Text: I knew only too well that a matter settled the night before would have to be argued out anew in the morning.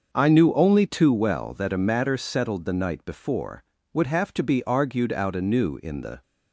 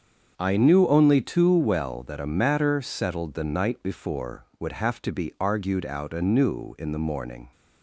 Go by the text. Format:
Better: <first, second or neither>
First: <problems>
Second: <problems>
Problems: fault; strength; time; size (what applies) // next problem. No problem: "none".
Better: second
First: starts louder than the rest; until 1.1 s; 6.5 dB // stops before "morning"; at 6.2 s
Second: starts louder than the rest; until 1.3 s; 7 dB